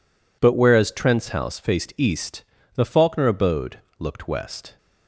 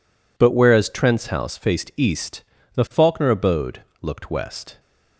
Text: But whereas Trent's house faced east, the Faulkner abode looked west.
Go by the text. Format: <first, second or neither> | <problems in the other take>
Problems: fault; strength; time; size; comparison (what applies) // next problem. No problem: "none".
neither | pauses between "abode" and "looked"; slight; the same in both